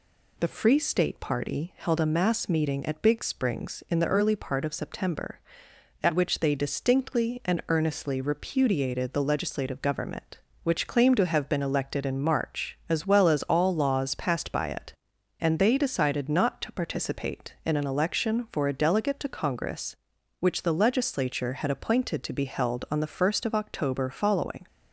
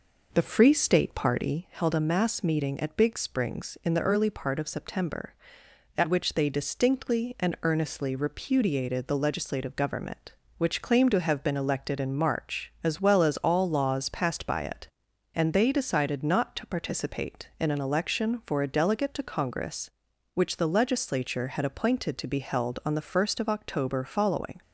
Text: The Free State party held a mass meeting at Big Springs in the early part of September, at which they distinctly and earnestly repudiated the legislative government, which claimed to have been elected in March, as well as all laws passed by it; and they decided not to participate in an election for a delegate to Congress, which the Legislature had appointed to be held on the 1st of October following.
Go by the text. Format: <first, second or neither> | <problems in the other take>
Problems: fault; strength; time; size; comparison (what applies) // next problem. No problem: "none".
first | starts louder than the rest; noticeable; until 1.6 s; 5 dB